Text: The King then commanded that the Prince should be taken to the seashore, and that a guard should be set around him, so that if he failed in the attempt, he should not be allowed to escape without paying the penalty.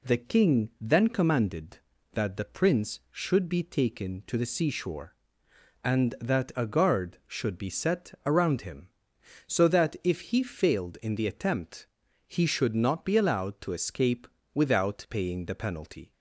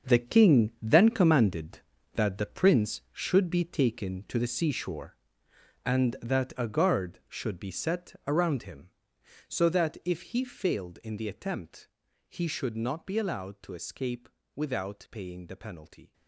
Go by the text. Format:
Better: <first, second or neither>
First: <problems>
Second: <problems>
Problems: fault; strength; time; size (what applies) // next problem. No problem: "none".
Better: first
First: pauses between "escape" and "without"; slight; at 14.2 s; 0.26 s long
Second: gets quieter; strong; throughout; 12 dB // pauses between "escape" and "without"; slight; at 14.2 s; 0.26 s long